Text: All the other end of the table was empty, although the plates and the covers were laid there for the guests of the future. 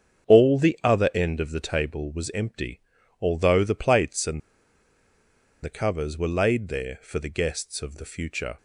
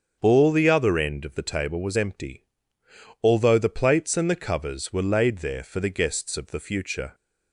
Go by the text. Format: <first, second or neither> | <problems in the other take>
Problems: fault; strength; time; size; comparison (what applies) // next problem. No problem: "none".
second | starts louder than the rest; strong; until 1.3 s; 7.5 dB; strong in the second // pauses between "and" and "the"; at 4.4 s; 1.2 s long